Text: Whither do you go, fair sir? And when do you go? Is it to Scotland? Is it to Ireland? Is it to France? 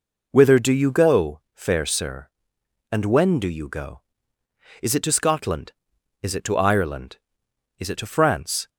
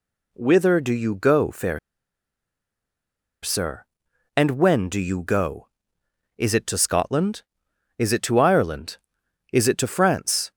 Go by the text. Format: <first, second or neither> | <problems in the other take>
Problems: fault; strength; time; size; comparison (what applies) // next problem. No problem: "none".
first | pauses between "fair" and "sir"; strong; at 1.7 s; 1.6 s long